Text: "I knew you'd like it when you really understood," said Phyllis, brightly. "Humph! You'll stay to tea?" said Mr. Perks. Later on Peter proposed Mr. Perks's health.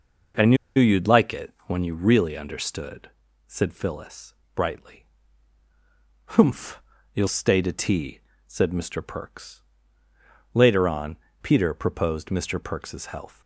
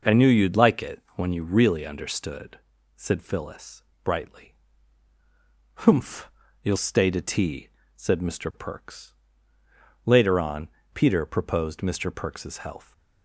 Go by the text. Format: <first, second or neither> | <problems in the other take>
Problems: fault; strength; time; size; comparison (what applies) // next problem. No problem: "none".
second | pauses between "knew" and "you'd"; slight; at 0.5 s; 0.22 s long // pauses between "on" and "Peter"; slight; at 11.1 s; 0.26 s long; slight in the second